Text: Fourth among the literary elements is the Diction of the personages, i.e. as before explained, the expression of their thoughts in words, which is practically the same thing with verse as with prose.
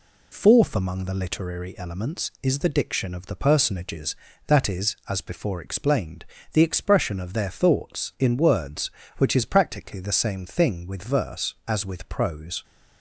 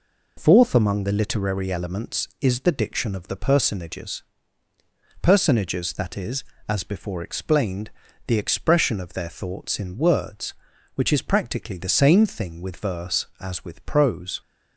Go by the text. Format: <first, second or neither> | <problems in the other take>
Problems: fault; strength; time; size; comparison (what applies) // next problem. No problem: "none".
first | says "personages" twice; at 5.2 s